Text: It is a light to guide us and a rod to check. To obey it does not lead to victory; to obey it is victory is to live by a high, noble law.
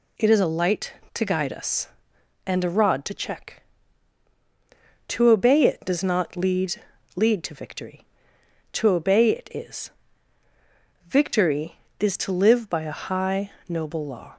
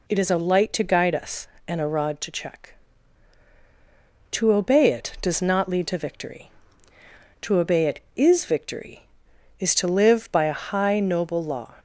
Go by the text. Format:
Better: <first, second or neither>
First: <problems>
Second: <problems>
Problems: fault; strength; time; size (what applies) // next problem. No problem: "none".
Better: second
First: says "lead" twice; at 7.1 s // pauses between "is" and "victory"; at 9.9 s; 1.1 s long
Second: none